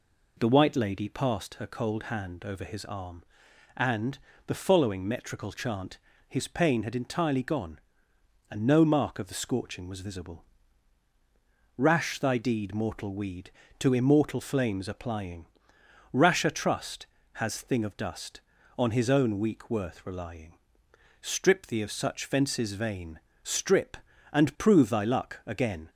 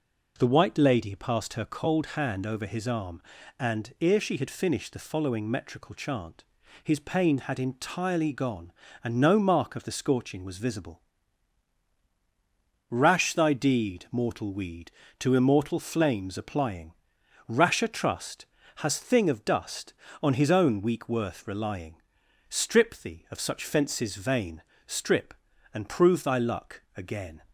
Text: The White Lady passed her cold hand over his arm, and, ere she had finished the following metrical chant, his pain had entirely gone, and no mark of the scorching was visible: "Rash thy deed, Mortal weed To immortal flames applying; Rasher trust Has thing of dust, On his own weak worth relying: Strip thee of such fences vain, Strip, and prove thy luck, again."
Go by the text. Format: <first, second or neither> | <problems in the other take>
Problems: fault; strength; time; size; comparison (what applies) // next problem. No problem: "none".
second | skips "ere she had finished"; at 4.3 s